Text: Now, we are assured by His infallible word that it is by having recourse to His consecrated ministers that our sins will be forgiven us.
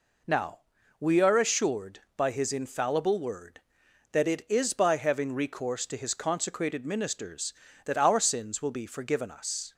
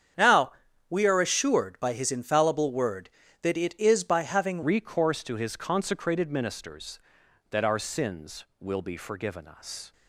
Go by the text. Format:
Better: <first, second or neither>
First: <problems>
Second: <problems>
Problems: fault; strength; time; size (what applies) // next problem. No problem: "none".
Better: first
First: none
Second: starts louder than the rest; strong; until 1.5 s; 8 dB // changes voice at "recourse"; from 4.6 s on; 5.3 s long